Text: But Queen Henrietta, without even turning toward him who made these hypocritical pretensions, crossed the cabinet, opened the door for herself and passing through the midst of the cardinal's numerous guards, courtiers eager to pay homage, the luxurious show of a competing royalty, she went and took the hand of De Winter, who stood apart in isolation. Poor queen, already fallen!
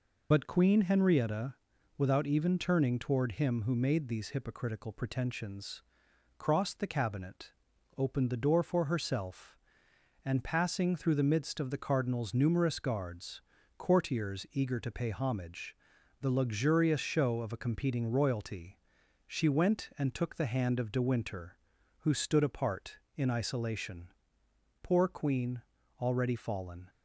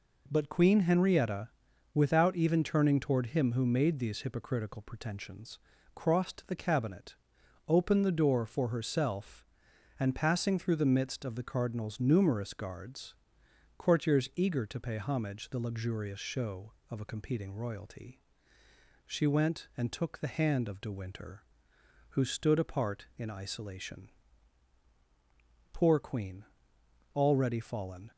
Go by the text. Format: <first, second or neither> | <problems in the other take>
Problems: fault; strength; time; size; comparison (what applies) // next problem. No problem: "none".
second | loses the start of "But"; at 0.3 s; 50 ms